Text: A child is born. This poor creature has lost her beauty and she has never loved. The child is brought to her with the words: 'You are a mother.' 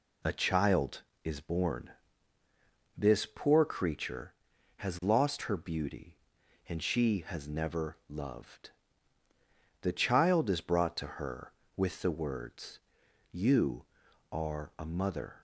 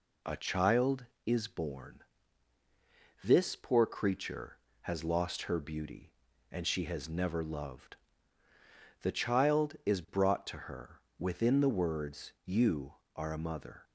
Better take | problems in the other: first | says "within" for "with"; at 11.1 s

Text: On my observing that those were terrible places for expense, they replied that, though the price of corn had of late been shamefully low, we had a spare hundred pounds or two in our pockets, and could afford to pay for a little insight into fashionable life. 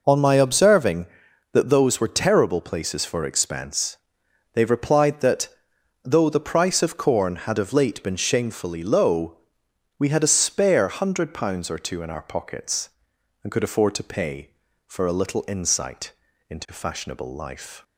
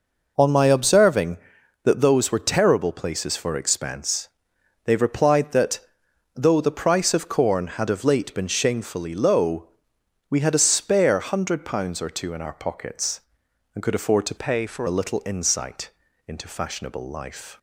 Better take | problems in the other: first | changes voice from "pay" to "for"; from 14.3 to 14.8 s; 0.5 s long // pauses between "insight" and "into"; at 15.8 s; 0.38 s long; also in the first

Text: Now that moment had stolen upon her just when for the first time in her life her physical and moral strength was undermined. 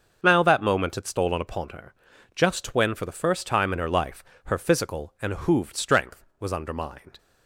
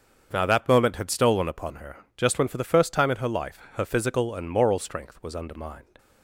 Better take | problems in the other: second | starts louder than the rest; until 1.2 s; 6.5 dB; also in the second // pauses between "her" and "just"; at 1.9 s; 0.42 s long; slight in the second // pauses between "life" and "her"; slight; at 4.2 s; 0.22 s long // says "hooved" for "moral"; at 5.3 s

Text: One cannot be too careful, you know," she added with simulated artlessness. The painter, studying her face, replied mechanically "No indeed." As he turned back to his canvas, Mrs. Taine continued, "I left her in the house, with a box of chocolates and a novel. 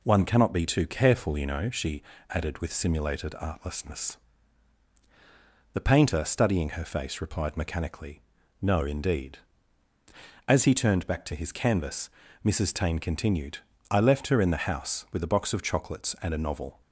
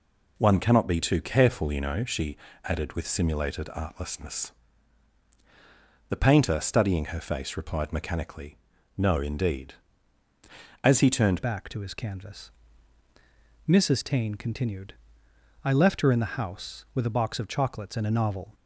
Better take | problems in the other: first | pauses between "she" and "added"; slight; at 2.3 s; 0.28 s long; slight in the first // pauses between "mechanically" and "No"; at 8.5 s; 0.40 s long; also in the first // changes voice at "back"; from 11.4 s on; 7.1 s long

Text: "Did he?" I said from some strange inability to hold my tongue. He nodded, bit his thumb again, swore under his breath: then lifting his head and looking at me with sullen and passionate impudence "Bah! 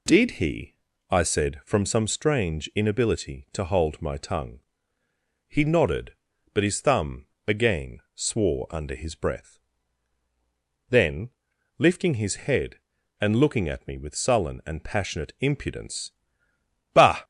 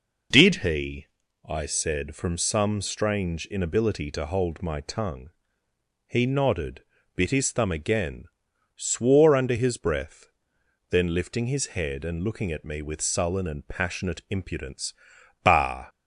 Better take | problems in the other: second | says "but" for "bit"; at 6.5 s // pauses between "thumb" and "again"; slight; at 7.2 s; 0.18 s long // pauses between "then" and "lifting"; noticeable; at 11.3 s; 0.46 s long // pauses between "impudence" and "Bah"; noticeable; at 16.1 s; 0.80 s long; noticeable in the second

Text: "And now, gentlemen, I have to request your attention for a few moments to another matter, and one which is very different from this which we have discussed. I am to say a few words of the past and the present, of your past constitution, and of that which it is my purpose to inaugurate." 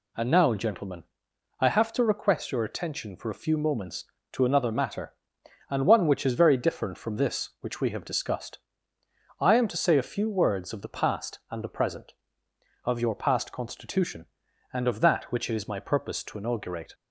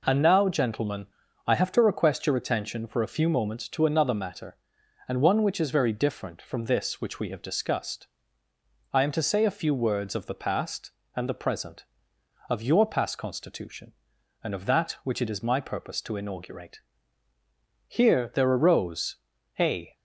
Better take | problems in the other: first | goes on to say "Here there arose a"; strong; from 17.9 s on; 2.0 s long

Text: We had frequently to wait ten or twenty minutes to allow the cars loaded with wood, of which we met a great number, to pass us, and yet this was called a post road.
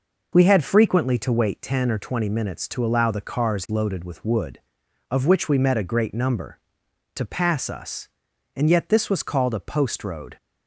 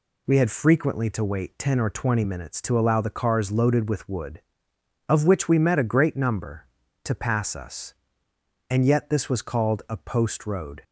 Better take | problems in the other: neither | none

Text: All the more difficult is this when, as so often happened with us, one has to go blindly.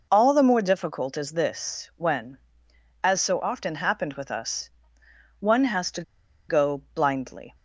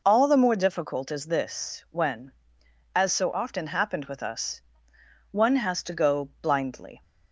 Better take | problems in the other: second | pauses between "to" and "go"; noticeable; at 6.0 s; 0.46 s long

